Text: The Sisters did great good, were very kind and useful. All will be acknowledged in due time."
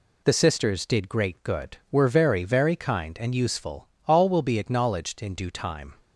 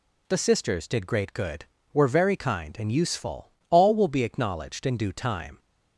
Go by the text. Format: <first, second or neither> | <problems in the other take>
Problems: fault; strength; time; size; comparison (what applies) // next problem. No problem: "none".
second | says "very" twice; at 2.4 s